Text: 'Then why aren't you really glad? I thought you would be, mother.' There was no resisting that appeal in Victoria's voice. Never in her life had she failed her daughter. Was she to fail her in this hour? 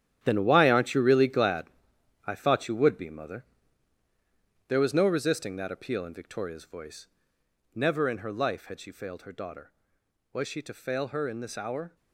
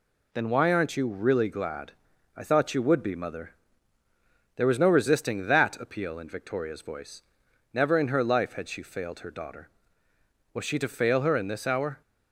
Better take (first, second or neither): second